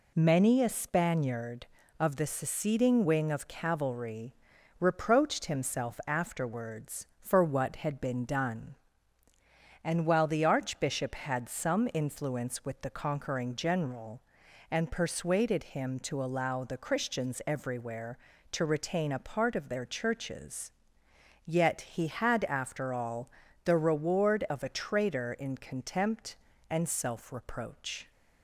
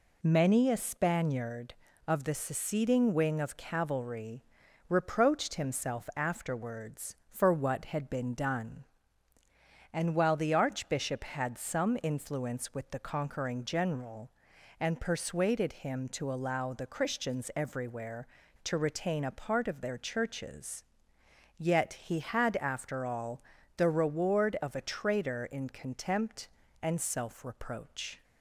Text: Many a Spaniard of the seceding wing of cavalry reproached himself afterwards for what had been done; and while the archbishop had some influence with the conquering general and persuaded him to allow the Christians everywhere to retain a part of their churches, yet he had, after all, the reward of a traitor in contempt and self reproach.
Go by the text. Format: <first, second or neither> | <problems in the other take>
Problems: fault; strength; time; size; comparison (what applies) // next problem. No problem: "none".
neither | pauses between "cavalry" and "reproached"; the same in both